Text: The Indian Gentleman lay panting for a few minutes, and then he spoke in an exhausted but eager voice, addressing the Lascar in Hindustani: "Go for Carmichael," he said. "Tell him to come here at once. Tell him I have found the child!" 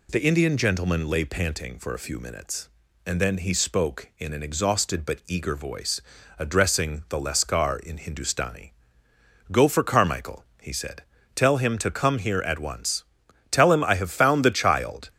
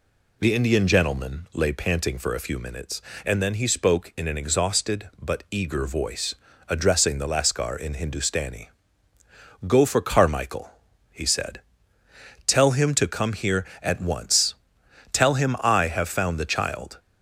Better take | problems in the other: neither | none

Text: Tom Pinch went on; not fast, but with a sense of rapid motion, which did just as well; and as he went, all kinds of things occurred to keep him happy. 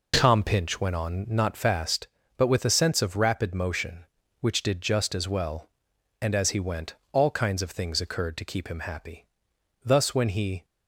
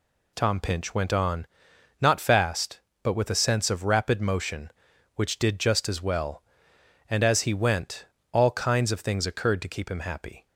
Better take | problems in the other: second | goes on to say "Thus when he"; noticeable; from 9.8 s on; 0.82 s long

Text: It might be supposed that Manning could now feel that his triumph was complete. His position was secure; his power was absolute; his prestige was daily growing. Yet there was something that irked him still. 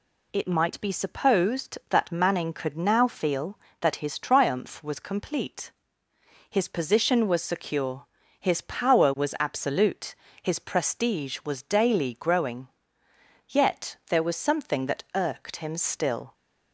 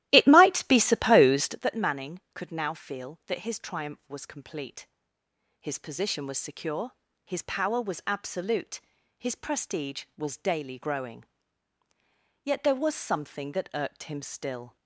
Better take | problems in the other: first | starts louder than the rest; strong; until 1.6 s; 15 dB

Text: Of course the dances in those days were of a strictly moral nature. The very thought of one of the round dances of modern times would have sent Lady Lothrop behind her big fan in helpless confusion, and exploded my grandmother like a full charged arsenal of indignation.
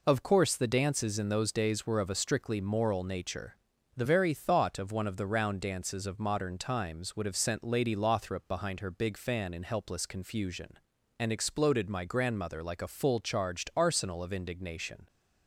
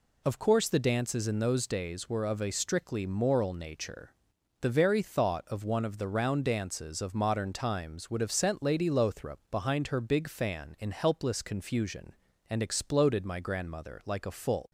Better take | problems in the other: first | stops before "charged arsenal of indignation"; at 14.6 s

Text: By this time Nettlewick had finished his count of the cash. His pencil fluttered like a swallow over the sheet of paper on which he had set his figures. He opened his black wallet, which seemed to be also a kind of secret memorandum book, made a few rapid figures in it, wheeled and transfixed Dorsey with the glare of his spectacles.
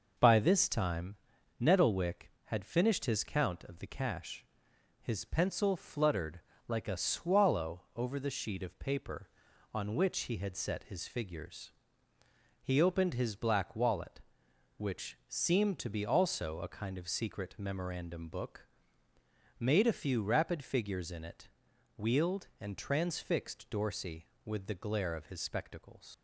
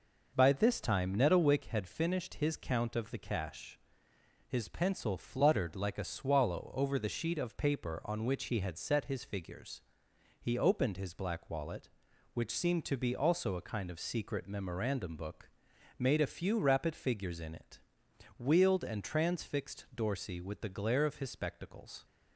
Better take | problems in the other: second | pauses between "time" and "Nettlewick"; at 1.1 s; 0.44 s long // pauses between "fluttered" and "like"; slight; at 6.3 s; 0.28 s long // leaves "spectacles" unfinished; at 26.1 s; 85 ms

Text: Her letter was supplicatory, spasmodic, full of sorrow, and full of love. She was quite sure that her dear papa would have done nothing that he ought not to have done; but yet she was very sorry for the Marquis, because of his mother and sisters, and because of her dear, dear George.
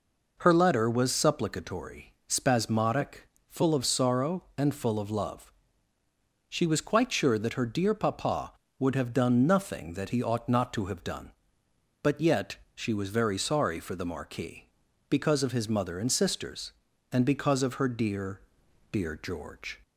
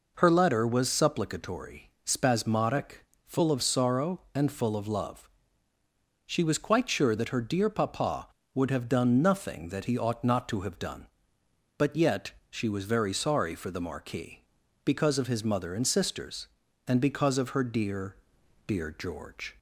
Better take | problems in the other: neither | pauses between "yet" and "she"; slight; the same in both

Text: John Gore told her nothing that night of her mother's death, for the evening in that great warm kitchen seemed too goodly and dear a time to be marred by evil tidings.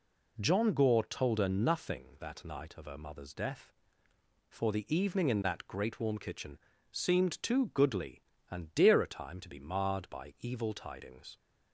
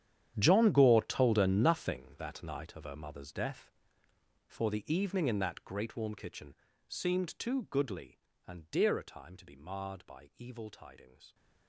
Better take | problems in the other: first | gets quieter; strong; throughout; 16 dB // pauses between "kitchen" and "seemed"; slight; at 6.5 s; 0.34 s long; slight in the first

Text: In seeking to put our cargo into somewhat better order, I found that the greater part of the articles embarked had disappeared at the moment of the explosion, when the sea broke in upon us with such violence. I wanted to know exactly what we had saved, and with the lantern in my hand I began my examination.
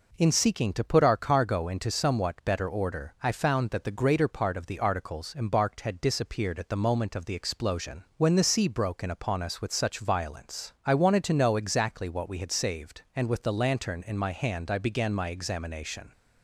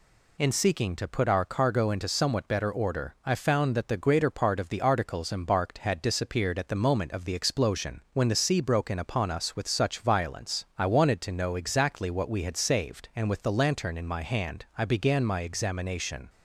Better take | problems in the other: neither | none

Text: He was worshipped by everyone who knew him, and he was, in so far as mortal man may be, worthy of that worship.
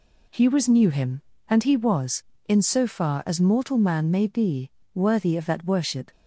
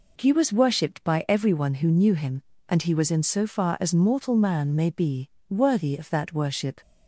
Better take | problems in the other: second | skips "worshipped by everyone who"; at 0.6 s

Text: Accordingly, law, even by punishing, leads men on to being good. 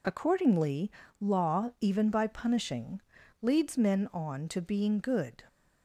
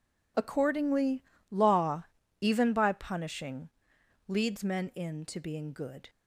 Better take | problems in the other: first | says "in" for "on"; at 4.9 s

